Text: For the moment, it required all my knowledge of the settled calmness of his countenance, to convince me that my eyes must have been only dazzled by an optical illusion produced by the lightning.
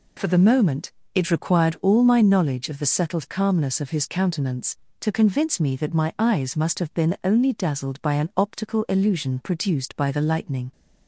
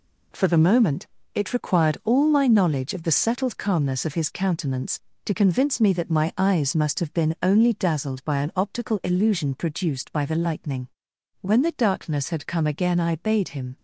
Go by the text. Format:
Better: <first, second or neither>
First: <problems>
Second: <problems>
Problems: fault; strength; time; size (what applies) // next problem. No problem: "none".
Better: first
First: none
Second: goes on to say "When the darkness had come again I bade him"; strong; from 11.4 s on; 2.3 s long